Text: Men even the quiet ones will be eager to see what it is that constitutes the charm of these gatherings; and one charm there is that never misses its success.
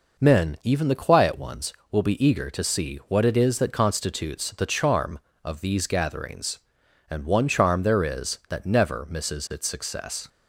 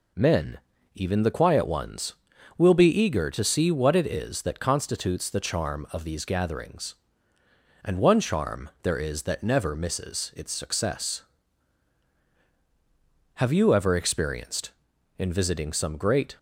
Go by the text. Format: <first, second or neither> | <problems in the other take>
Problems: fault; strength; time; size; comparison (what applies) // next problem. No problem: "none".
first | pauses between "Men" and "even"; slight; at 0.5 s; 0.34 s long // goes on to say "Have you ever experienced in visiting some great"; strong; from 13.3 s on; 3.0 s long